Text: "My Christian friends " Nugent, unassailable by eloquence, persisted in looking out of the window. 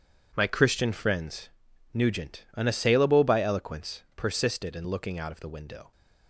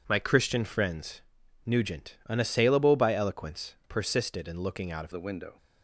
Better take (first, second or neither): first